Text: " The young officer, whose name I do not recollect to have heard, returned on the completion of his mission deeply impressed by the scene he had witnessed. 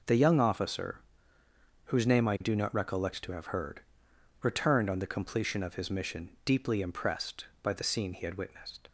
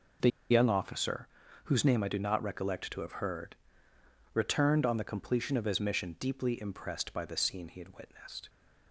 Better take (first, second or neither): first